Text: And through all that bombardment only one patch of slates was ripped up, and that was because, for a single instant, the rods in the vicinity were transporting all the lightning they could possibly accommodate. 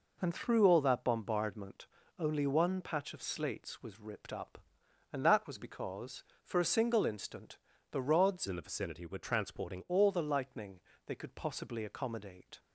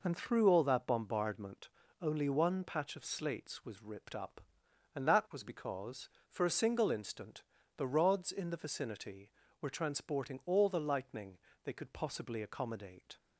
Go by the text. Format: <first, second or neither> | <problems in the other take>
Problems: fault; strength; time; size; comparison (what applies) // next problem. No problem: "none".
second | pauses between "bombardment" and "only"; slight; at 1.8 s; 0.32 s long; slight in the second // changes voice from "in" to "transporting"; from 8.4 to 9.8 s; 1.4 s long // pauses between "lightning" and "they"; slight; at 10.8 s; 0.24 s long; slight in the second